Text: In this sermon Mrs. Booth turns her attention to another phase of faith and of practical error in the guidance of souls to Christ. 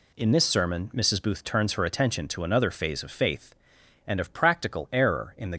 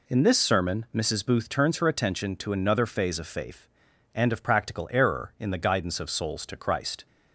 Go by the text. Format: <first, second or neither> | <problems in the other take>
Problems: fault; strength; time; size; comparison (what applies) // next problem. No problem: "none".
second | stops before "guidance of souls to Christ"; at 5.5 s